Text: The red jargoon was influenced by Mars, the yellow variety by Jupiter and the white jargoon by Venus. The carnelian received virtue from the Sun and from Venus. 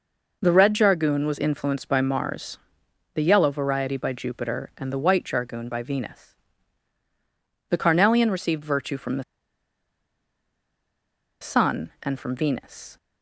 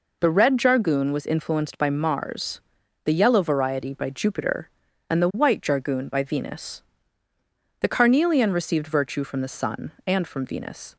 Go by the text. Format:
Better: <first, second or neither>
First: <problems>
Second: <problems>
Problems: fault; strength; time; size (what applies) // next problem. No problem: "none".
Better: second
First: pauses between "the" and "Sun"; strong; at 9.2 s; 2.1 s long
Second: none